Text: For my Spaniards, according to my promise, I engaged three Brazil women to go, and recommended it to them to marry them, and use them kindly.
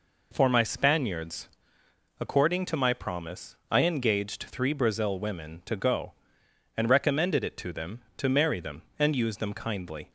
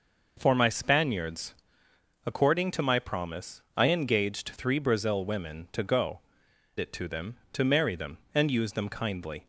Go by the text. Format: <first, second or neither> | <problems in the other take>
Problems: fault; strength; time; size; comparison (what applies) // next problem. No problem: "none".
first | skips "and recommended"; at 6.4 s